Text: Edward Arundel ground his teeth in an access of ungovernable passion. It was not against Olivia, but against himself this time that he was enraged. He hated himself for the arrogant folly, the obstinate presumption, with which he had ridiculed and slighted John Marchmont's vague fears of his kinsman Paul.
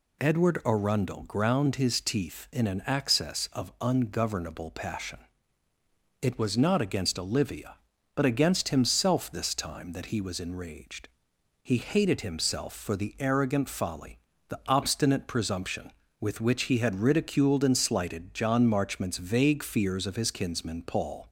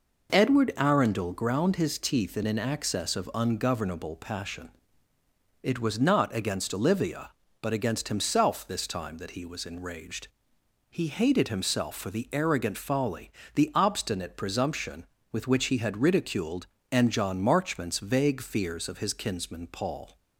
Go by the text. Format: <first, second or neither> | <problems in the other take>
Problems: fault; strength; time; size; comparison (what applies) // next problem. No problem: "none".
first | skips "slighted"; at 17.1 s